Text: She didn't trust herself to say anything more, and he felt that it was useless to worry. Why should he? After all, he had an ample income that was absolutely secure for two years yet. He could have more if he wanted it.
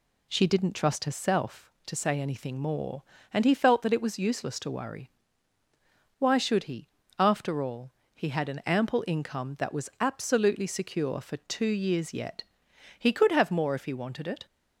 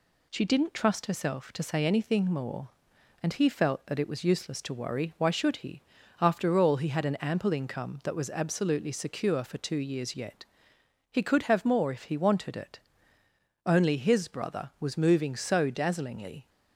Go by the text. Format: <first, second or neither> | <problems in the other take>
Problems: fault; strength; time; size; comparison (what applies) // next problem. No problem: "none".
first | goes on to say "Only his brother was moving so dazzlingly"; strong; from 13.6 s on; 2.8 s long